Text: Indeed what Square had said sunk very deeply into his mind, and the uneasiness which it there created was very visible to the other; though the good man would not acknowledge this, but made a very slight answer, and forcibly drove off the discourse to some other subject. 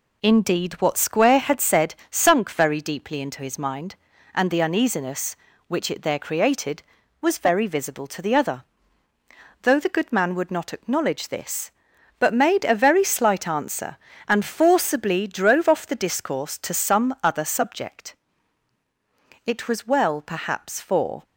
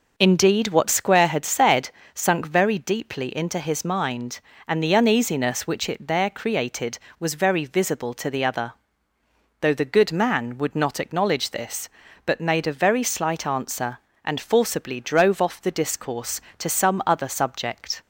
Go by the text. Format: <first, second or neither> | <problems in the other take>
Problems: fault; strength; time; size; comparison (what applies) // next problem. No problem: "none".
second | pauses between "said" and "sunk"; slight; at 1.9 s; 0.16 s long; slight in the second // goes on to say "It was well perhaps for"; strong; from 19.4 s on; 1.7 s long